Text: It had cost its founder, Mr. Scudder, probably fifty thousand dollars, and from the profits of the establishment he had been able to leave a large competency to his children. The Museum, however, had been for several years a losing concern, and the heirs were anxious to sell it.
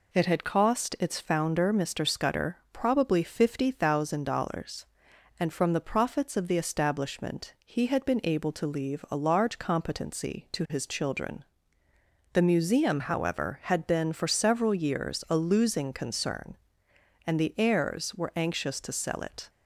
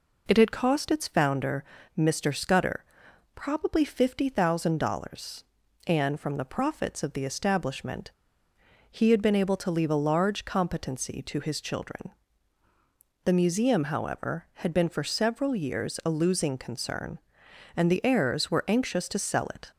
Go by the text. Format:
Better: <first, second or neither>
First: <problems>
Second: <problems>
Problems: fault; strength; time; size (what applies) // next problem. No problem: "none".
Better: first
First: none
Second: pauses between "establishment" and "he"; noticeable; at 8.1 s; 0.79 s long